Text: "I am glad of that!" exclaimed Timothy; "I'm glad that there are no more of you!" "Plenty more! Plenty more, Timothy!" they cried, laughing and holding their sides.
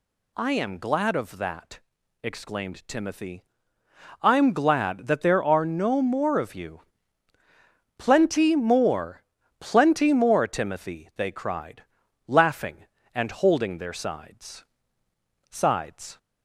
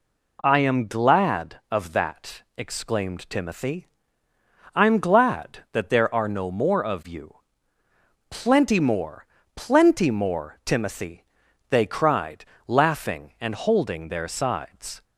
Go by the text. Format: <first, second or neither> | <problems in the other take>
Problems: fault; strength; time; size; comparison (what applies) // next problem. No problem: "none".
second | says "sides" twice; at 15.4 s